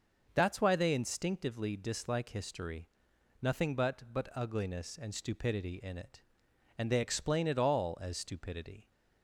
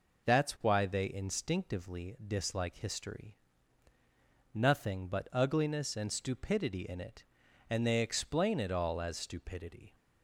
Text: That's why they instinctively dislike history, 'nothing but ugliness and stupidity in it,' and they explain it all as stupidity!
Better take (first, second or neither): second